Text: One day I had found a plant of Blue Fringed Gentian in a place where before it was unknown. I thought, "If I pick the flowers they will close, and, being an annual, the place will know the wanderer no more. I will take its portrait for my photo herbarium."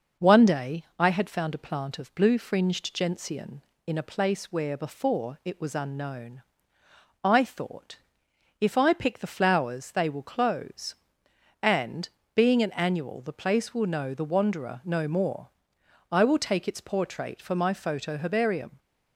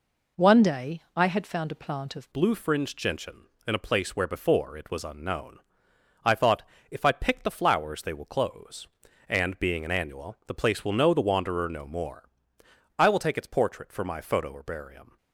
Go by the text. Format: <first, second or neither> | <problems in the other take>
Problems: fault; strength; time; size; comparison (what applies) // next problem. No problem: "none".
first | changes voice at "Blue"; from 2.3 s on; 12.8 s long